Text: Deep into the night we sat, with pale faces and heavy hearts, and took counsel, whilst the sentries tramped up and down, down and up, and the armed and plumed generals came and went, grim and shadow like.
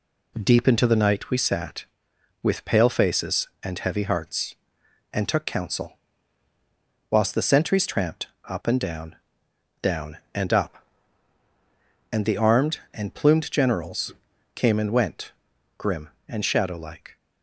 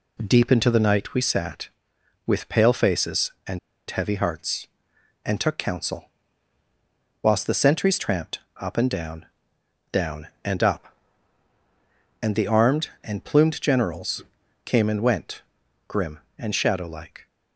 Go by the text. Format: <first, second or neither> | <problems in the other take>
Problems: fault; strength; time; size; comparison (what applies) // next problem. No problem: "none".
first | pauses between "and" and "heavy"; slight; at 3.5 s; 0.31 s long // pauses between "tramped" and "up"; slight; at 8.4 s; 0.20 s long; slight in the first // pauses between "generals" and "came"; at 14.2 s; 0.44 s long; also in the first